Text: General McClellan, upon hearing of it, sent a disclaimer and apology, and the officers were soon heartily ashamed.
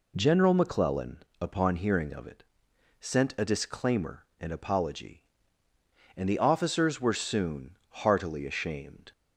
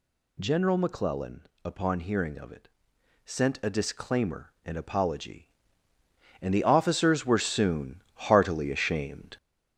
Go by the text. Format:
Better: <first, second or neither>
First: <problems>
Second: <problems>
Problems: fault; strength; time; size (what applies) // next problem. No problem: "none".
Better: first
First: none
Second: gets louder; throughout; 4 dB